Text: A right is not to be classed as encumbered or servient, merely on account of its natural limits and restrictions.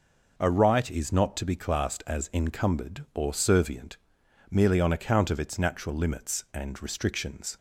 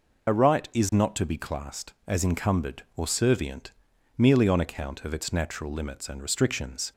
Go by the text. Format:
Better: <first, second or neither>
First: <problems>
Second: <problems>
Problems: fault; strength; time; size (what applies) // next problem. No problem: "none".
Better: first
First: none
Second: loses the start of "A"; at 0.2 s; 40 ms